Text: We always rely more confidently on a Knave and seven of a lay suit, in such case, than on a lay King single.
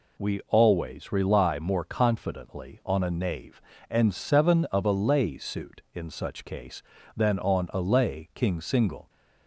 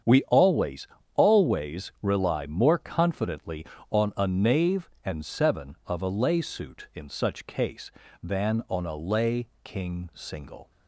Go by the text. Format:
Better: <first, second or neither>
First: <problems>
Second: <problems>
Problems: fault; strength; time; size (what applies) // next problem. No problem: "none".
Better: first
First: none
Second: starts louder than the rest; strong; until 1.4 s; 8 dB // says "always" twice; at 1.1 s // pauses between "lay" and "King"; slight; at 9.4 s; 0.16 s long